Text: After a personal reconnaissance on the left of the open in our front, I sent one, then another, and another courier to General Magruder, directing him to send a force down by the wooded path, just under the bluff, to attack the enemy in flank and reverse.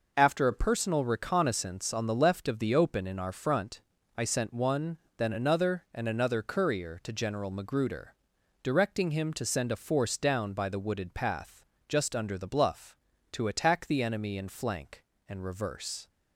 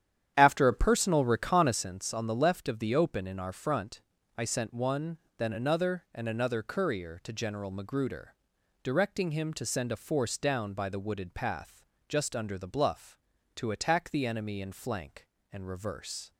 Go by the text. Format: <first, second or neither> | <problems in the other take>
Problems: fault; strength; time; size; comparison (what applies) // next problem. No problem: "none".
first | starts louder than the rest; strong; until 1.9 s; 10 dB